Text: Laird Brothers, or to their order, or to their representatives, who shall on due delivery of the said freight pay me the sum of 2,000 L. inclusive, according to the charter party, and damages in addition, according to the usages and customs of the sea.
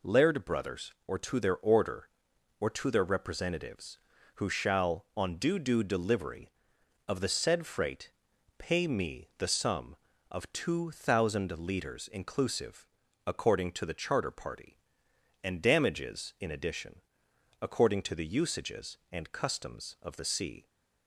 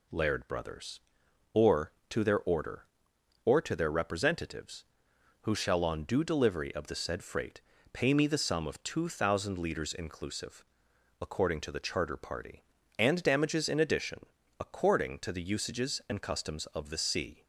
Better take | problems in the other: second | says "due" twice; at 5.5 s // pauses between "freight" and "pay"; noticeable; at 8.1 s; 0.46 s long; slight in the second

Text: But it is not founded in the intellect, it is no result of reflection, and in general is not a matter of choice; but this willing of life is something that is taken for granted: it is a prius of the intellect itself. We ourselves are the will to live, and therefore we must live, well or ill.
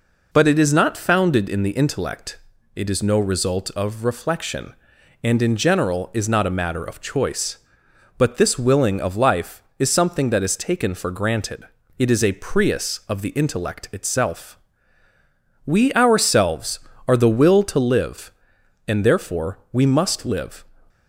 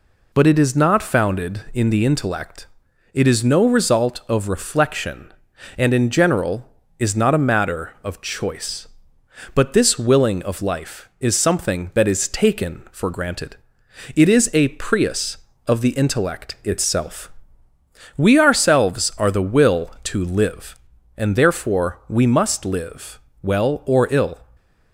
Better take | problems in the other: second | stops before "well or ill"; at 20.8 s

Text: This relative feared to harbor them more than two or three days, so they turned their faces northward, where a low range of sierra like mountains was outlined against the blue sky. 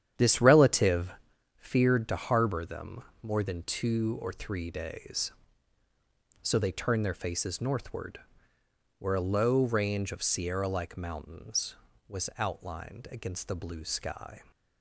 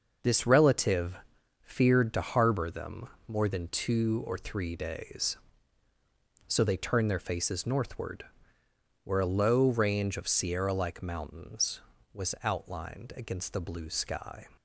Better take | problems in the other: second | starts louder than the rest; strong; until 1.3 s; 9.5 dB // pauses between "relative" and "feared"; noticeable; at 1.0 s; 0.48 s long; noticeable in the second // pauses between "them" and "more"; slight; at 3.0 s; 0.22 s long; slight in the second

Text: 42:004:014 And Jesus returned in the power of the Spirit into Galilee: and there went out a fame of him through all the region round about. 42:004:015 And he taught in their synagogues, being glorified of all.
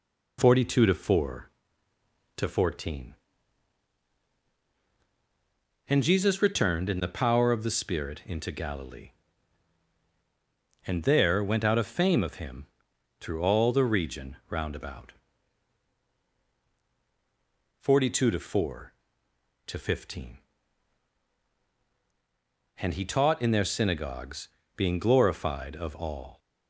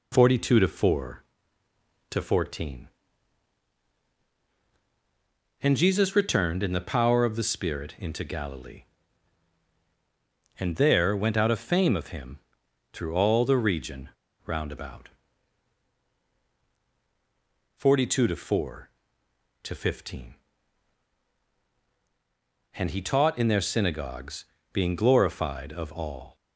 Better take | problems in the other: first | pauses between "him" and "through"; noticeable; at 12.3 s; 0.56 s long; noticeable in the first // pauses between "region" and "round"; slight; at 14.0 s; 0.35 s long

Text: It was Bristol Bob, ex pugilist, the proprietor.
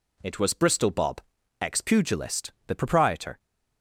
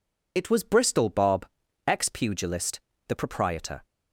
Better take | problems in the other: first | loses the start of "It"; at 0.3 s; 55 ms

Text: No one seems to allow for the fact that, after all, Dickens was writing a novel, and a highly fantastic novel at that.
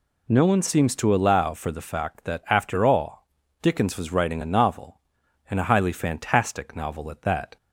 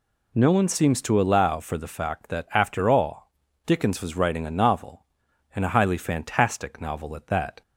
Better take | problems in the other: neither | none

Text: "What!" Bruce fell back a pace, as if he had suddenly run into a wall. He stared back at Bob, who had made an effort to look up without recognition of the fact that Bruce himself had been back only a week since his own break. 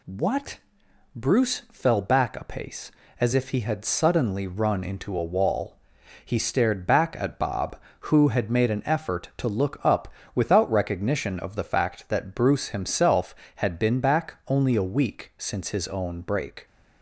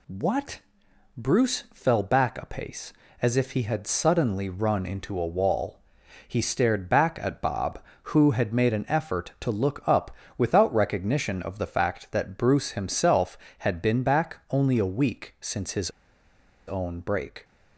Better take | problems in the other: first | pauses between "up" and "without"; slight; at 10.1 s; 0.22 s long; slight in the first // pauses between "his" and "own"; noticeable; at 15.9 s; 0.77 s long

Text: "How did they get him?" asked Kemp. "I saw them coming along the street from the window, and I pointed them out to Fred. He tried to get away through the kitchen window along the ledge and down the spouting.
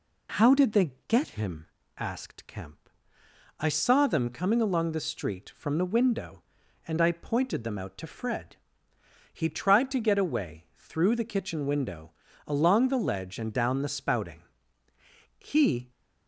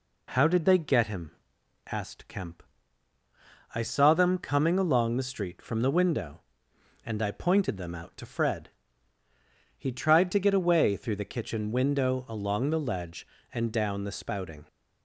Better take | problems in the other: second | pauses between "they" and "get"; slight; at 0.9 s; 0.16 s long // pauses between "window" and "along"; slight; at 12.1 s; 0.34 s long // goes on to say "He"; from 15.3 s on; 0.54 s long

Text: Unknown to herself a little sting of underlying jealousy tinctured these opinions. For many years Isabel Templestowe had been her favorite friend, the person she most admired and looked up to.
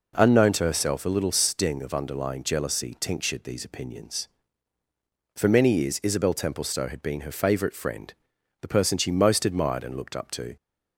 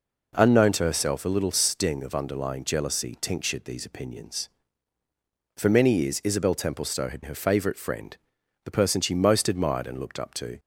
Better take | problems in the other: first | skips "been"; at 7.2 s

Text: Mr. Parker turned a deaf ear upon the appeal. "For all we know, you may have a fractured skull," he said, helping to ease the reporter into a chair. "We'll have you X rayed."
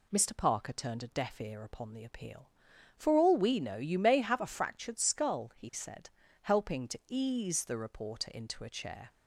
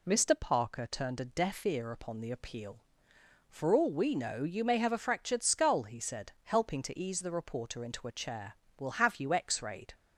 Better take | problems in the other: second | stops before "We'll have you X rayed"; at 9.0 s

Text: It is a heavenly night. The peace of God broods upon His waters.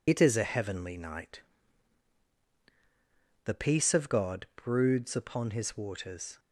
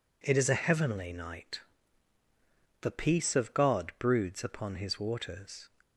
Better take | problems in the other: second | loses the start of "It"; at 0.0 s; 55 ms

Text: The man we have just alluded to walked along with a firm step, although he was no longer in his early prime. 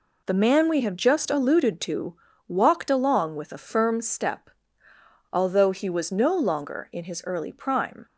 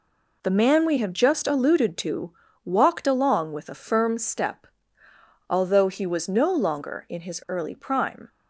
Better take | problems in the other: neither | pauses between "to" and "walked"; slight; the same in both

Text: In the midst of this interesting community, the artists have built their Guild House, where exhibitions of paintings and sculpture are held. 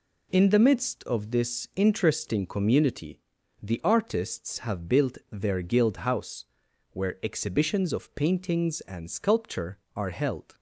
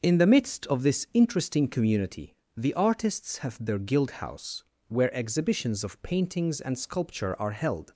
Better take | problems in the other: first | skips "built"; at 3.6 s

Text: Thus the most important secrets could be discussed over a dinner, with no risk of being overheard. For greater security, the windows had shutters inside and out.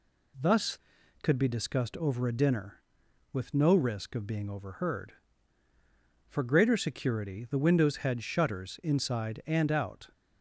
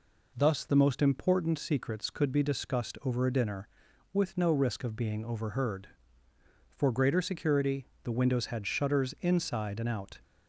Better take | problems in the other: second | skips "the most important secrets"; at 0.9 s

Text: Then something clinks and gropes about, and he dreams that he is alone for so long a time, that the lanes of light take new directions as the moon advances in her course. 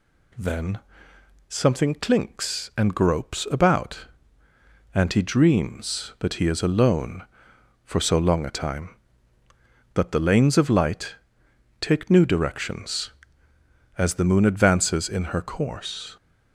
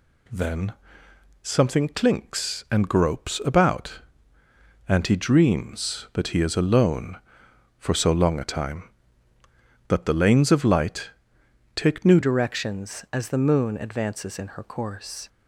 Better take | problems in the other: first | pauses between "Then" and "something"; noticeable; at 0.7 s; 0.68 s long; noticeable in the first // pauses between "light" and "take"; noticeable; at 11.1 s; 0.64 s long; noticeable in the first // changes voice at "directions"; from 12.2 s on; 3.0 s long

